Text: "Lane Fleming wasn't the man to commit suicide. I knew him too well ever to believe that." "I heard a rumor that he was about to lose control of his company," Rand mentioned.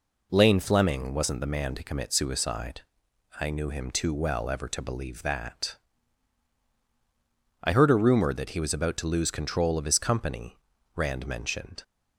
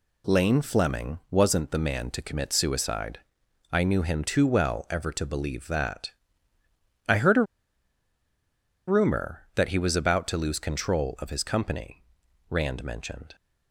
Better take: first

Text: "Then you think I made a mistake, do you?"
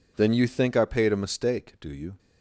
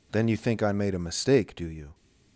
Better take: second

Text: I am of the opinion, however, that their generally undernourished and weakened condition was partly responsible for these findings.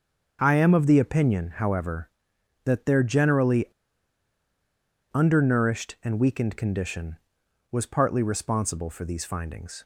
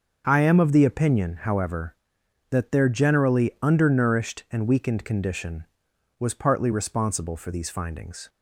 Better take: second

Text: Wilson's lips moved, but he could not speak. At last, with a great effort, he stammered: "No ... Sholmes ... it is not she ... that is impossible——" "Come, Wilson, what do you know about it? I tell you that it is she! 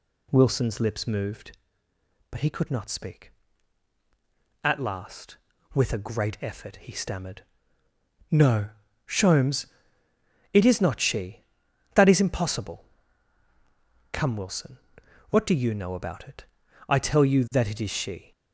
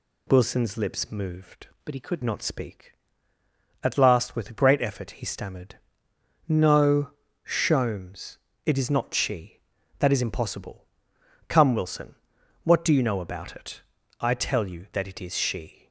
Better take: first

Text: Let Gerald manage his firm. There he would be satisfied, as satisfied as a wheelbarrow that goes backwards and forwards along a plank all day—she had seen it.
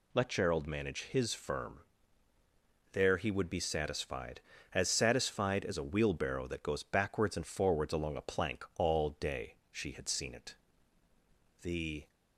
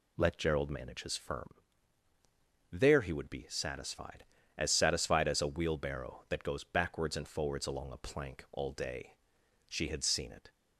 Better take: second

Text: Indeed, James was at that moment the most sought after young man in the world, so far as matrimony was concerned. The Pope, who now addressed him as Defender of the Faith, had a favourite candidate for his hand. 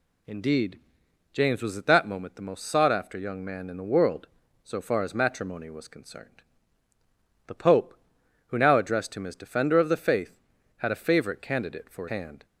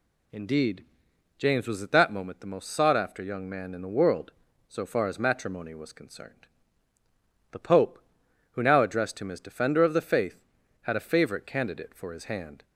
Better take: second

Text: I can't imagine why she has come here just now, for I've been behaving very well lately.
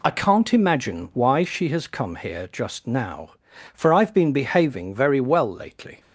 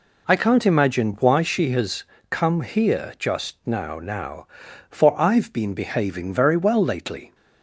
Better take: first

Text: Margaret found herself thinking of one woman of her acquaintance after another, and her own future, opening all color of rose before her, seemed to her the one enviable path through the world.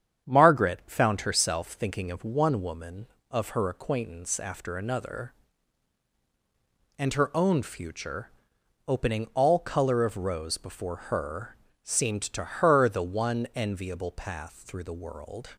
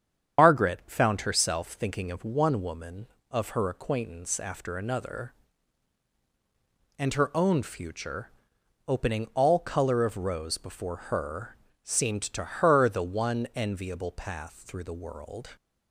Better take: first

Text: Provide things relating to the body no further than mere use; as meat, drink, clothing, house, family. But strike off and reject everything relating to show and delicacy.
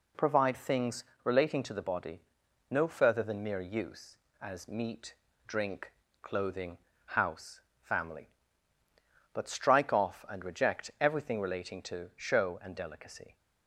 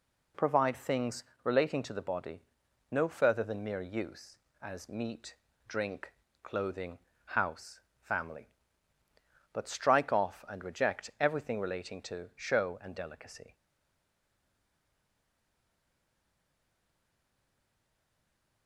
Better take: first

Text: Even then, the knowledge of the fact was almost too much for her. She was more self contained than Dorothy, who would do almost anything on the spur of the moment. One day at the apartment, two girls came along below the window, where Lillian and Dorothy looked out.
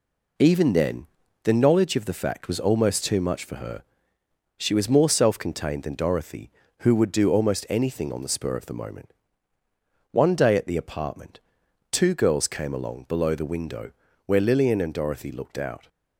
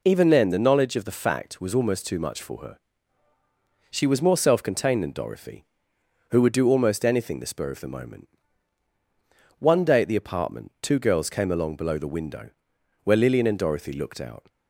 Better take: first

